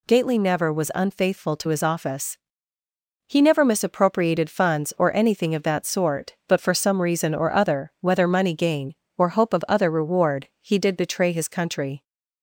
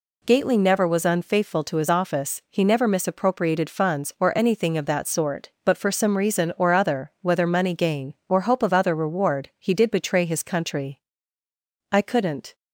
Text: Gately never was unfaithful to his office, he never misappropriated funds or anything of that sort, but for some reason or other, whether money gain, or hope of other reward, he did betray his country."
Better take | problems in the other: first | goes on to say "I couldn't"; noticeable; from 11.9 s on; 0.62 s long

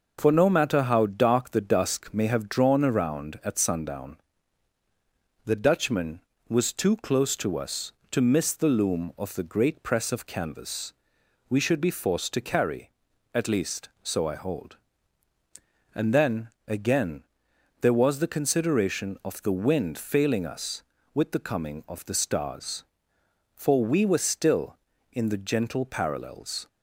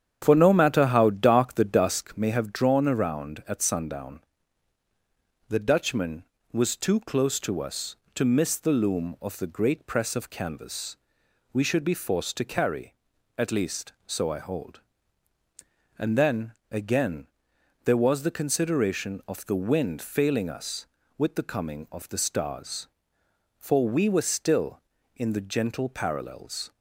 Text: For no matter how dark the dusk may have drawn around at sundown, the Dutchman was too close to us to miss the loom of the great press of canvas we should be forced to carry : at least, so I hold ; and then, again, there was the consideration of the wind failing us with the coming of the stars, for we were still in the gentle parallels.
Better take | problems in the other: first | starts louder than the rest; strong; until 2.0 s; 9 dB // pauses between "canvas" and "we"; noticeable; at 10.9 s; 0.56 s long; noticeable in the first

